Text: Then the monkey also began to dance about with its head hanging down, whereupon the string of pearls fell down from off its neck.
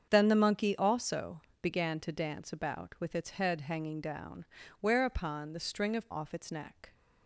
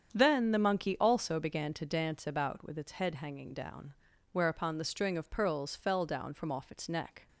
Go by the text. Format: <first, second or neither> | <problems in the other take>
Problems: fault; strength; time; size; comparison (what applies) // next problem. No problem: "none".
second | starts louder than the rest; strong; until 1.1 s; 7.5 dB; strong in the second // pauses between "also" and "began"; slight; at 1.3 s; 0.22 s long // skips "pearls fell down from"; at 6.1 s